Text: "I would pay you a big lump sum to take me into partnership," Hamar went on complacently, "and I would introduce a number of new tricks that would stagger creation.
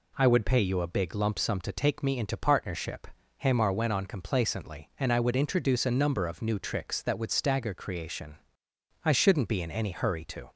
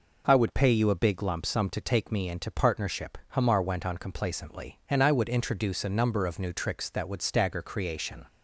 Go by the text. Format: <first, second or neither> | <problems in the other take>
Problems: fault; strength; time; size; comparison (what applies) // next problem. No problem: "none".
second | goes on to say "I shouldn't be in any hurry to"; from 9.0 s on; 1.4 s long